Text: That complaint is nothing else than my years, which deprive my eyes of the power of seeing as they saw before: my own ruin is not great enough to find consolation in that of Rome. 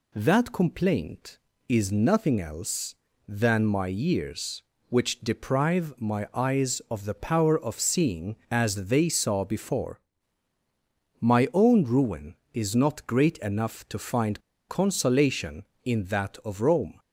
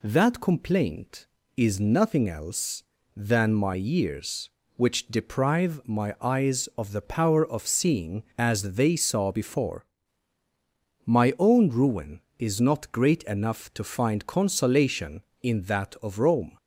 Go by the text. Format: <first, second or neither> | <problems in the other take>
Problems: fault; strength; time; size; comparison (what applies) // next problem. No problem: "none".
second | pauses between "find" and "consolation"; slight; at 14.3 s; 0.29 s long